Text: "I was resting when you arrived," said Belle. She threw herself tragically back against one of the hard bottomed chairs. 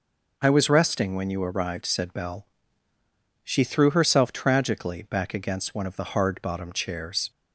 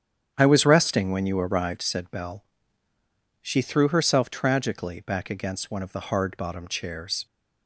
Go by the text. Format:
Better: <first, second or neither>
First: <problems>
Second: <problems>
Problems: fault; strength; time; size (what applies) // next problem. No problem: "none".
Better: first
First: none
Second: starts louder than the rest; strong; until 1.9 s; 8.5 dB